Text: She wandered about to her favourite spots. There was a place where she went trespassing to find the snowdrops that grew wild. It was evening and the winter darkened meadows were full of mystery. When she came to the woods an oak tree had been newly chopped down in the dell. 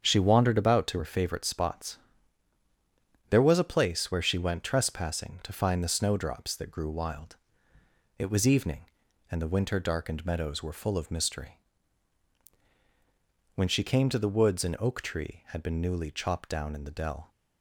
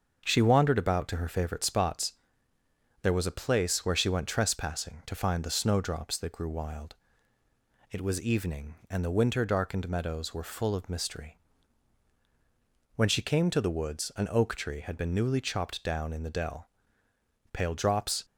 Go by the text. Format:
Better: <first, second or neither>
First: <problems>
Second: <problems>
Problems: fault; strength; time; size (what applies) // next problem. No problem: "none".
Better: first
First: starts louder than the rest; strong; until 1.0 s; 7.5 dB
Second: starts louder than the rest; until 1.2 s; 6.5 dB // goes on to say "Pale drops"; noticeable; from 17.5 s on; 0.74 s long